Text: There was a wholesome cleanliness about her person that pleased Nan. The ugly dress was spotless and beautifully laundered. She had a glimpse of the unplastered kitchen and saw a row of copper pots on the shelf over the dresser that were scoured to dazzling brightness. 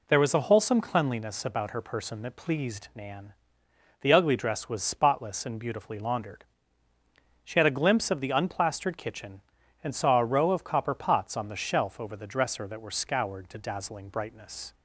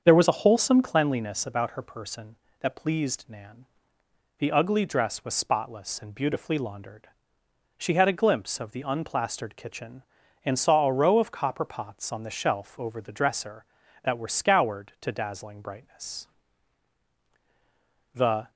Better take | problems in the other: first | starts louder than the rest; strong; until 1.0 s; 7 dB // goes on to say "The"; slight; from 18.1 s on; 0.36 s long

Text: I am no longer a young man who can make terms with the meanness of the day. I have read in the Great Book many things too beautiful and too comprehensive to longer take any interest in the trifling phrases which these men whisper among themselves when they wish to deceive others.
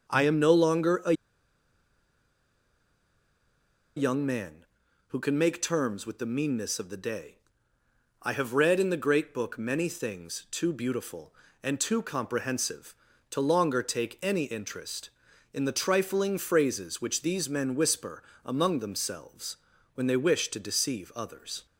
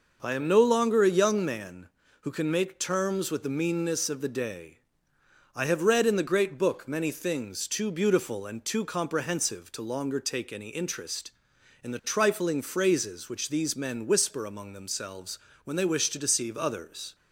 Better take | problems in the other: second | starts louder than the rest; until 1.1 s; 6 dB // pauses between "a" and "young"; strong; at 1.1 s; 2.8 s long // pauses between "whisper" and "among"; slight; at 18.2 s; 0.24 s long // pauses between "themselves" and "when"; at 19.5 s; 0.40 s long; slight in the second

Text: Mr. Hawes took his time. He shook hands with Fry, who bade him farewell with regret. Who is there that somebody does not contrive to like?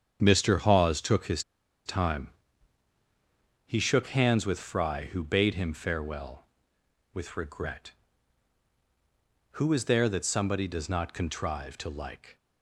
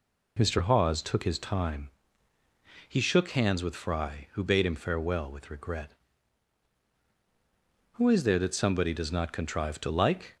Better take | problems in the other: second | starts louder than the rest; strong; until 1.2 s; 8 dB // pauses between "his" and "time"; at 1.4 s; 0.44 s long

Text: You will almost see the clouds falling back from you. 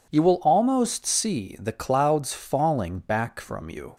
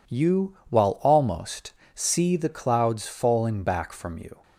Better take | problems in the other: first | says "while" for "will"; at 0.6 s // pauses between "almost" and "see"; slight; at 1.7 s; 0.22 s long

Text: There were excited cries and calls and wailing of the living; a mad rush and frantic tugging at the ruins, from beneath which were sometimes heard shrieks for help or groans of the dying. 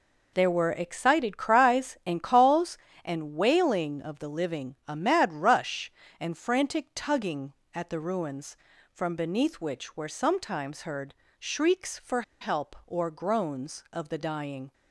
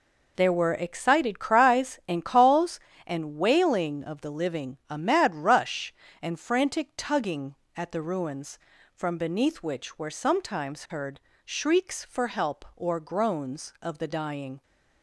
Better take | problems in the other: second | pauses between "heard" and "shrieks"; slight; at 11.1 s; 0.24 s long; slight in the second // pauses between "for" and "help"; slight; at 12.2 s; 0.18 s long

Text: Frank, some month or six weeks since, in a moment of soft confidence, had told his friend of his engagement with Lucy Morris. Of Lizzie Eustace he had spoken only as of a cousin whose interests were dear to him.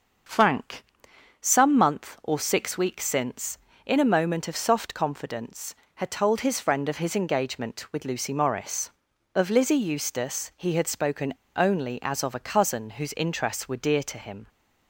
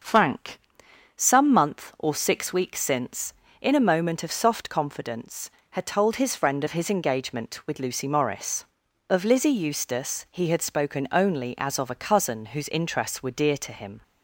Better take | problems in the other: second | starts louder than the rest; until 1.8 s; 6.5 dB; also in the second // pauses between "spoken" and "only"; slight; at 11.3 s; 0.22 s long

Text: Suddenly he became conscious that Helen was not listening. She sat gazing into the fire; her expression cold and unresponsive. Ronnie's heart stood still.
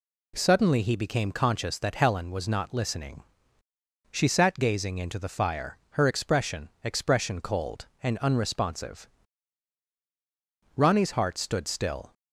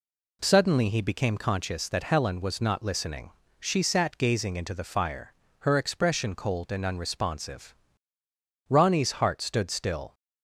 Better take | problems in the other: second | says "expression" twice; at 6.8 s

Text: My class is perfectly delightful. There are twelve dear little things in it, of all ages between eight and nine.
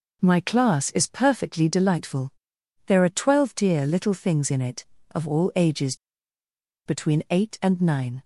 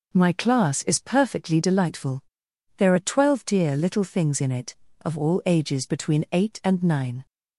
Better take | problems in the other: second | pauses between "ages" and "between"; noticeable; at 5.9 s; 0.90 s long

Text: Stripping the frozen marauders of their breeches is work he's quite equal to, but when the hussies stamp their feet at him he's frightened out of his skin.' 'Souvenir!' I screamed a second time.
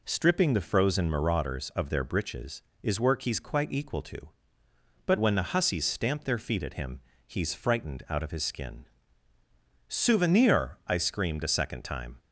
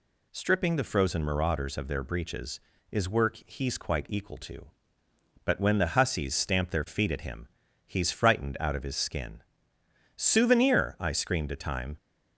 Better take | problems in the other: first | pauses between "him" and "he's"; at 7.4 s; 0.40 s long; slight in the first // skips "second"; at 11.5 s

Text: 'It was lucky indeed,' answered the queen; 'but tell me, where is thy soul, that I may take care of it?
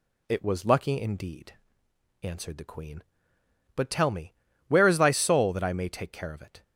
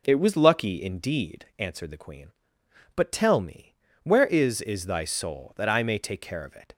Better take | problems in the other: first | says "is" twice; at 4.6 s

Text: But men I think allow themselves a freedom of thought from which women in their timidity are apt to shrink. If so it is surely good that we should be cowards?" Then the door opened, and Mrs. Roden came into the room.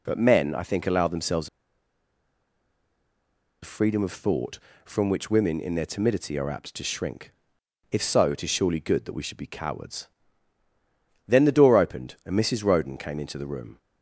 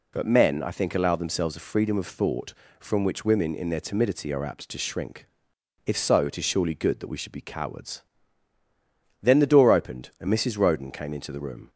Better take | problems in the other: second | pauses between "themselves" and "a"; strong; at 1.4 s; 2.1 s long

